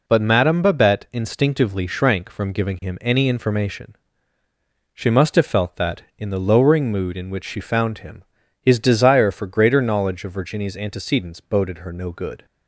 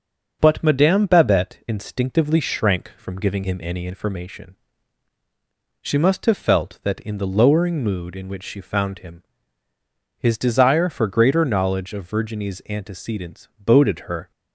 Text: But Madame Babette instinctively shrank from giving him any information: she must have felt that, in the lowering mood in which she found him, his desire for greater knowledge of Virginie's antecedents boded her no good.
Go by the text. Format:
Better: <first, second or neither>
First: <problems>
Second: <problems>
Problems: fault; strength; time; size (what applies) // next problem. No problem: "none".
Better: first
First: none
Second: starts louder than the rest; noticeable; until 1.4 s; 6 dB // stops before "no good"; at 14.3 s